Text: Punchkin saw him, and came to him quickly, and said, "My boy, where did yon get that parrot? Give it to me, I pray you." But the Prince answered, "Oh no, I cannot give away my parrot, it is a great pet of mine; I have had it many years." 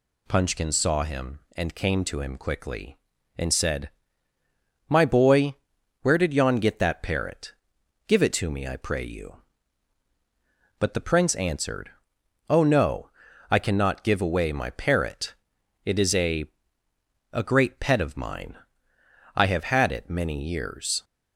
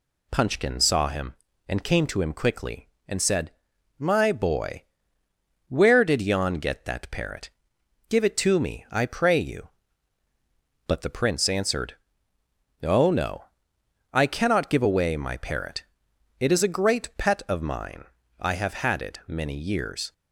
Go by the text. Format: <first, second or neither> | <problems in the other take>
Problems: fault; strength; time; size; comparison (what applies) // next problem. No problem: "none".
second | says "a" twice; at 17.3 s